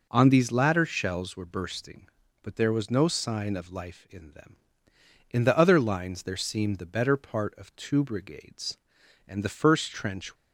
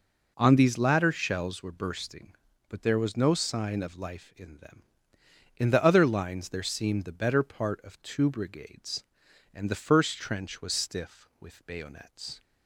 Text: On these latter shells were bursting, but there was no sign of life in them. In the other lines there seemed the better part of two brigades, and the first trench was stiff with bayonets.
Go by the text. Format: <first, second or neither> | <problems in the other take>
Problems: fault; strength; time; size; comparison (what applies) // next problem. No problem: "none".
second | stops before "was stiff with bayonets"; at 10.3 s